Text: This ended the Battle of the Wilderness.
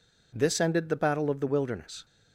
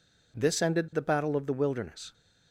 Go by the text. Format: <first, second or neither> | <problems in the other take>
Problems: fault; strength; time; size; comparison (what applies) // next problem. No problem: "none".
neither | none